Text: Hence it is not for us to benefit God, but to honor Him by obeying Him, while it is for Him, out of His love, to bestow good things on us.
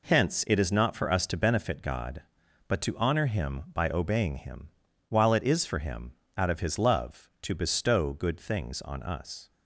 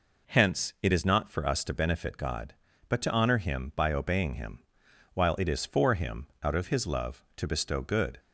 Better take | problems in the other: first | stops before "things on us"; at 8.1 s

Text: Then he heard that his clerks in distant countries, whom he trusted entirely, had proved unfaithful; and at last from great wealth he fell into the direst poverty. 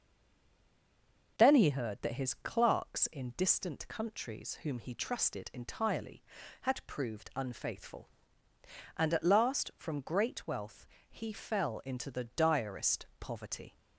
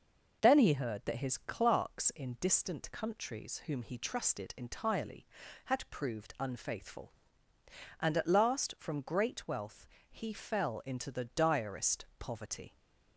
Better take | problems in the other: second | stays silent before the first word; noticeable; until 1.3 s; 1.3 s long // pauses between "wealth" and "he"; slight; at 10.8 s; 0.24 s long; slight in the second // pauses between "direst" and "poverty"; slight; at 13.0 s; 0.16 s long; slight in the second

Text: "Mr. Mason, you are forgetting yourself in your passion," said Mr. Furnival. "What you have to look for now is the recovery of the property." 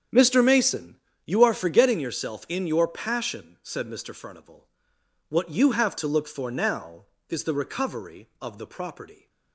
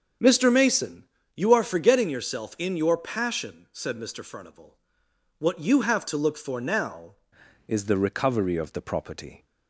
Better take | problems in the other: first | starts louder than the rest; until 1.4 s; 6 dB; strong in the first // changes voice at "is"; from 7.6 s on; 1.8 s long

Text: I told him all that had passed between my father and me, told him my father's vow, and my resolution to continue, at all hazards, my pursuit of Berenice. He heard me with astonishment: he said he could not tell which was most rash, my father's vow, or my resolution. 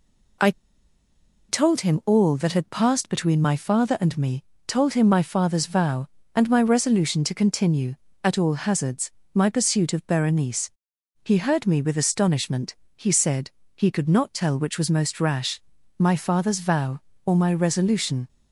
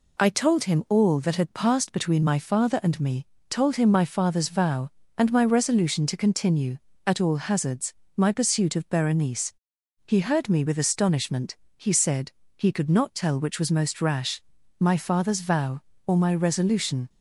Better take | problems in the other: second | pauses between "I" and "told"; at 0.5 s; 0.98 s long // pauses between "said" and "he"; slight; at 13.4 s; 0.26 s long; slight in the second

